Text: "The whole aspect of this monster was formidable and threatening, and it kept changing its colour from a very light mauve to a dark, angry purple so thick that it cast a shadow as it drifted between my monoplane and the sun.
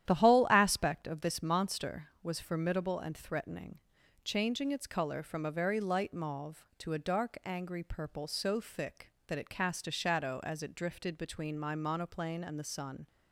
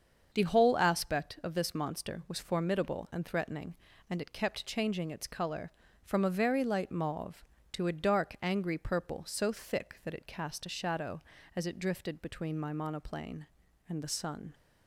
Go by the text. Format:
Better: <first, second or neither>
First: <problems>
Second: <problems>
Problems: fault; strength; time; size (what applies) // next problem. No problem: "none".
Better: second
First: starts louder than the rest; strong; until 1.1 s; 11 dB // skips "and it kept"; at 4.0 s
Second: starts louder than the rest; until 1.3 s; 7 dB